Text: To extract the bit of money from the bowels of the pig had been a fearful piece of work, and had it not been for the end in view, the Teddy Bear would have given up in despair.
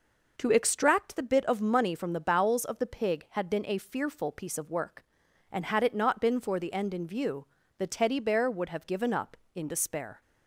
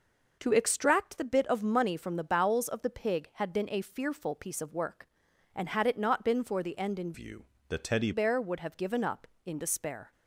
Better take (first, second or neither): first